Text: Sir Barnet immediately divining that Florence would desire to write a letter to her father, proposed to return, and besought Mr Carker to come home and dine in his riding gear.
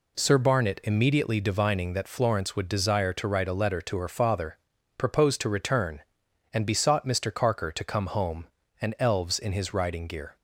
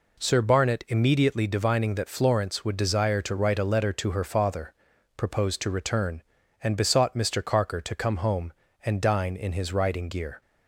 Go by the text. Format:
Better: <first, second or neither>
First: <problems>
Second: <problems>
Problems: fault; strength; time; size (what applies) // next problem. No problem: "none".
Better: second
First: says "elves" for "dine"; at 8.9 s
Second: none